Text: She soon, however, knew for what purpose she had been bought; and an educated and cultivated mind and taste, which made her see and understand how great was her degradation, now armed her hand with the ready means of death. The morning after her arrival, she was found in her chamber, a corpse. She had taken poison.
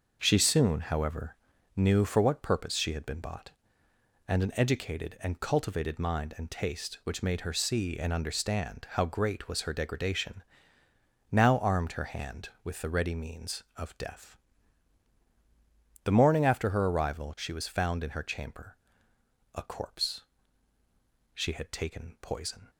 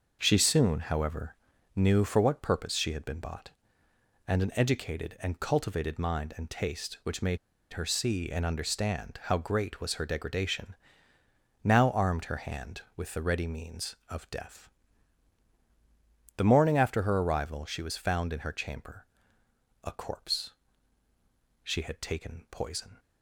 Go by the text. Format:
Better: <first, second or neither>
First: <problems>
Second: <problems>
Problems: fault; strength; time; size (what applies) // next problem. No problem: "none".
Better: first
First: starts louder than the rest; noticeable; until 1.2 s; 6 dB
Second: starts louder than the rest; noticeable; until 1.2 s; 6 dB // pauses between "made" and "her"; slight; at 7.3 s; 0.35 s long